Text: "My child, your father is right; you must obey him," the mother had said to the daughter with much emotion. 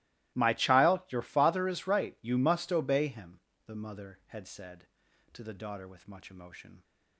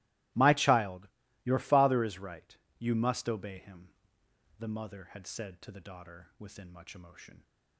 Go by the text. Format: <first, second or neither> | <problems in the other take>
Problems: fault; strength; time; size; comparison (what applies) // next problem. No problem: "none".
first | starts louder than the rest; strong; until 1.6 s; 19.5 dB; strong in the first // says "within" for "with"; at 6.3 s